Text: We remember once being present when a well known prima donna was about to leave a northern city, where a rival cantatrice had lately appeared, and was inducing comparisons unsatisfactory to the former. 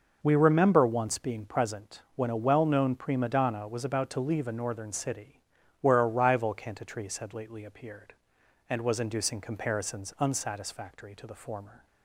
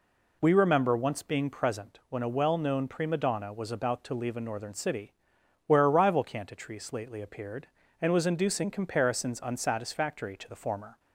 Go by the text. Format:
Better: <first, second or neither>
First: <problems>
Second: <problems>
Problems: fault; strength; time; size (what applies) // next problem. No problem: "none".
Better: first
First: none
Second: skips "had"; at 6.9 s